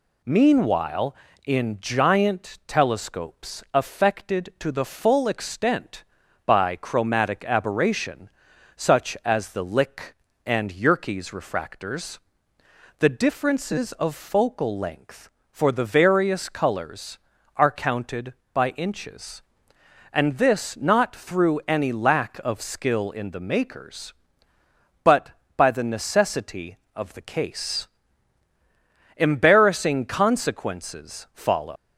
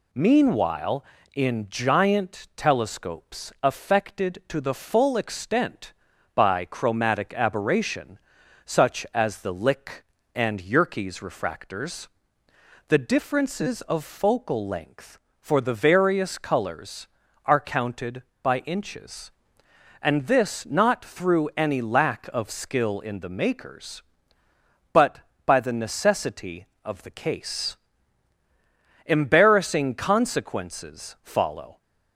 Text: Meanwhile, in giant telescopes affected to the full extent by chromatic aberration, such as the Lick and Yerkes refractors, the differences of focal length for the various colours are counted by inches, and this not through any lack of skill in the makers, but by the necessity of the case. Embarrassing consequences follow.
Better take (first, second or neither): second